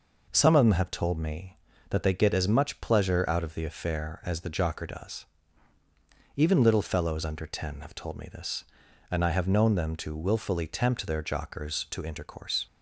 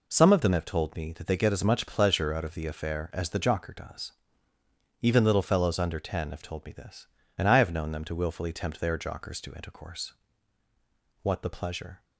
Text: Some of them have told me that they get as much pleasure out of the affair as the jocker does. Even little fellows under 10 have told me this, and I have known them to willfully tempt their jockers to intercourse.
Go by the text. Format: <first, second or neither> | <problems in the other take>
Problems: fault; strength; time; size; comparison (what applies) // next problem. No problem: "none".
first | goes on to say "What the pleasure"; noticeable; from 11.2 s on; 0.82 s long